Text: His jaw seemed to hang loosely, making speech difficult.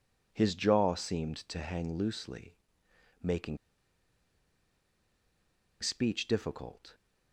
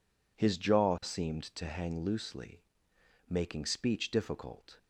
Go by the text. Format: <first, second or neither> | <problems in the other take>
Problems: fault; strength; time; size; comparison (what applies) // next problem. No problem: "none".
second | pauses between "making" and "speech"; strong; at 3.5 s; 2.2 s long